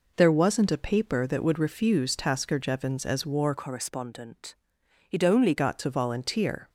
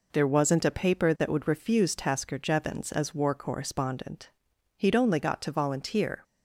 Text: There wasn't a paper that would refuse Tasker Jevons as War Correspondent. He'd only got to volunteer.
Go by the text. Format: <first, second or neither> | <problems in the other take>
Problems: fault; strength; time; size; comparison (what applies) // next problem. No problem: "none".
second | changes voice from "Correspondent" to "only"; from 3.5 to 5.5 s; 2.0 s long